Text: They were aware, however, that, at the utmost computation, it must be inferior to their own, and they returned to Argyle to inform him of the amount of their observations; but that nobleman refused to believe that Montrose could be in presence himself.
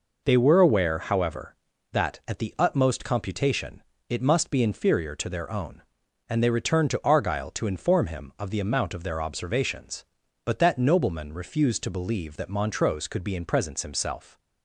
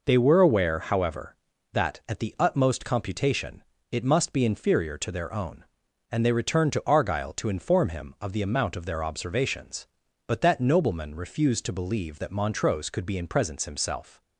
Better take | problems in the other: neither | none

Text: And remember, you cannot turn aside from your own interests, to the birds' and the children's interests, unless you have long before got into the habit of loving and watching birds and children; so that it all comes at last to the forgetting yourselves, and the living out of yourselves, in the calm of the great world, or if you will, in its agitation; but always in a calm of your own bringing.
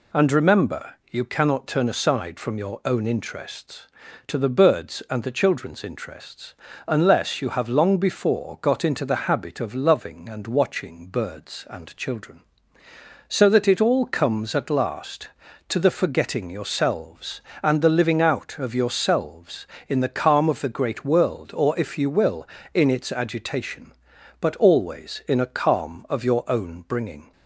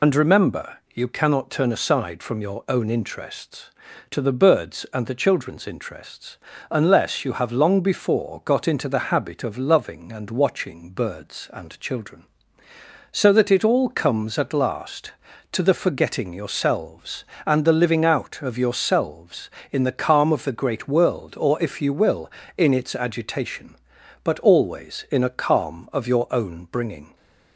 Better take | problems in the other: first | loses the start of "And"; at 0.0 s; 50 ms

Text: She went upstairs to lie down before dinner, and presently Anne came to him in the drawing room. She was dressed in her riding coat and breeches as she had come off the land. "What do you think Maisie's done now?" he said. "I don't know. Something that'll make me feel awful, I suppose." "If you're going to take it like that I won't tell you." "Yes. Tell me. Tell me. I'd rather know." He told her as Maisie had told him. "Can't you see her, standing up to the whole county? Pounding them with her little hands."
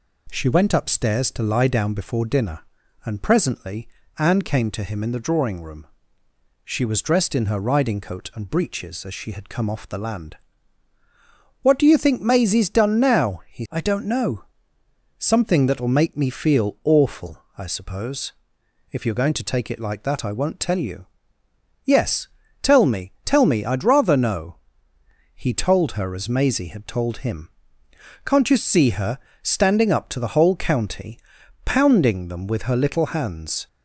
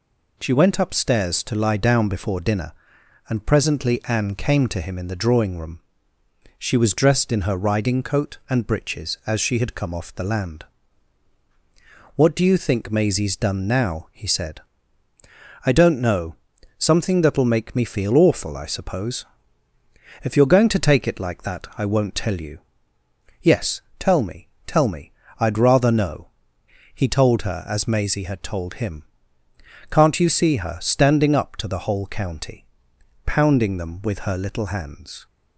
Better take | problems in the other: second | pauses between "presently" and "Anne"; slight; at 3.8 s; 0.30 s long // skips "said"; at 13.6 s

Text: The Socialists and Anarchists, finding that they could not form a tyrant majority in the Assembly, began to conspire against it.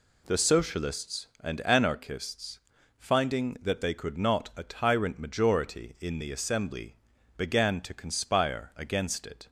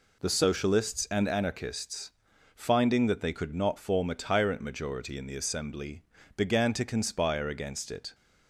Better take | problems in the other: second | skips "form"; at 4.5 s

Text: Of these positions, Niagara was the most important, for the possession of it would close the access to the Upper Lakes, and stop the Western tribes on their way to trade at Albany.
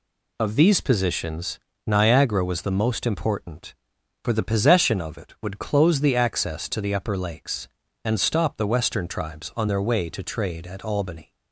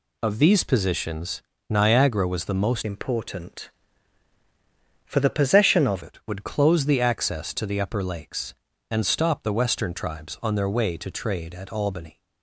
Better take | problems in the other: first | changes voice from "important" to "of"; from 2.8 to 6.0 s; 3.2 s long

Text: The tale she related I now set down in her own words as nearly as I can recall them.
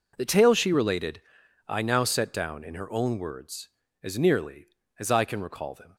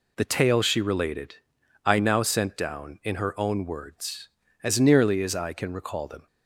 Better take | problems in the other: first | pauses between "related" and "I"; noticeable; at 1.3 s; 0.50 s long; noticeable in the first // says "sent" for "set"; at 2.2 s

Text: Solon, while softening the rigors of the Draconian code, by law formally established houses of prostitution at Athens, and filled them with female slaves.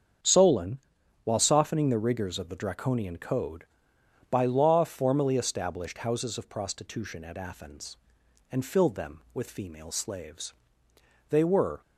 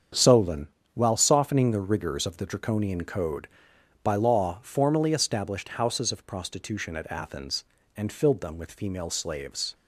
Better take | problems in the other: second | starts louder than the rest; strong; until 1.6 s; 7 dB; strong in the second // goes on to say "They were"; from 11.3 s on; 0.50 s long

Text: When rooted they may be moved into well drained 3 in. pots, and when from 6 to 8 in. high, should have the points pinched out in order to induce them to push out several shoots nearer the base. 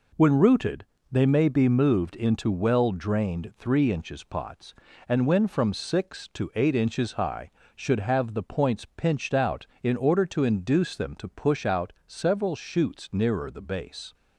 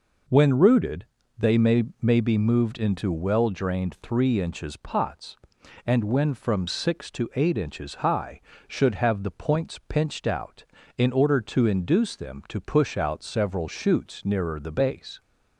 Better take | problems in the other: first | pauses between "rooted" and "they"; slight; at 1.0 s; 0.34 s long; slight in the first // says "may" twice; at 2.0 s

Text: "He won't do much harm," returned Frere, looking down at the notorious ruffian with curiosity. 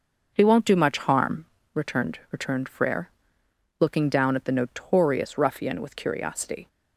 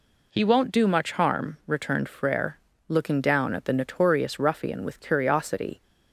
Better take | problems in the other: second | says "returned" twice; at 2.3 s

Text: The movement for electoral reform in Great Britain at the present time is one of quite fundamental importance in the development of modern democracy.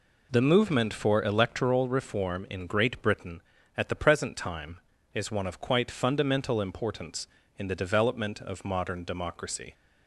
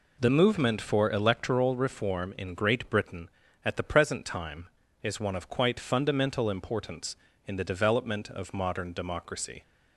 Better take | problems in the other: neither | none

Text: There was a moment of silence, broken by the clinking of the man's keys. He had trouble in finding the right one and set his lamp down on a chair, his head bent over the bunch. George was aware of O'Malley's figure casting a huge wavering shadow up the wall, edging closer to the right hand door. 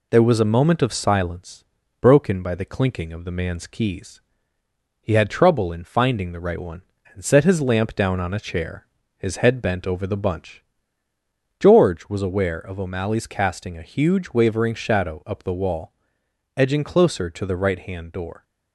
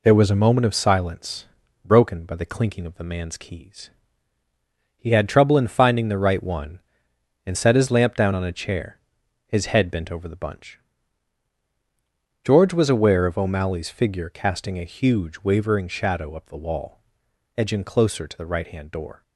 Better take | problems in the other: second | skips "figure"; at 13.2 s

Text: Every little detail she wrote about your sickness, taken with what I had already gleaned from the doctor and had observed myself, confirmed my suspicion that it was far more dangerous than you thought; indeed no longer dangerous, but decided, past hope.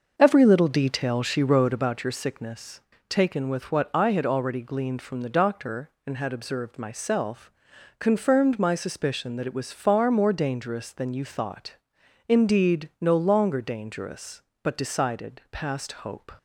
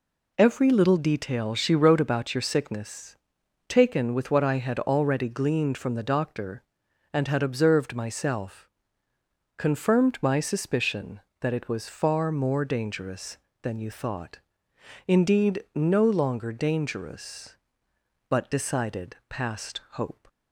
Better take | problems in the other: second | starts louder than the rest; until 2.0 s; 6 dB

